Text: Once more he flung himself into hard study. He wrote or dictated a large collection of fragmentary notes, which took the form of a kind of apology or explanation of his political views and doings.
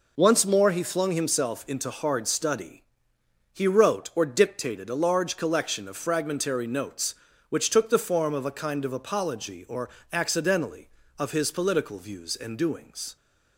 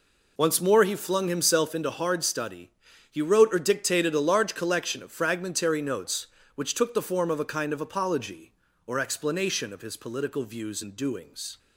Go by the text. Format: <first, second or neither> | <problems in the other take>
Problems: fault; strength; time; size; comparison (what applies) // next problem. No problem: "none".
second | says "accidentally" for "explanation"; at 10.1 s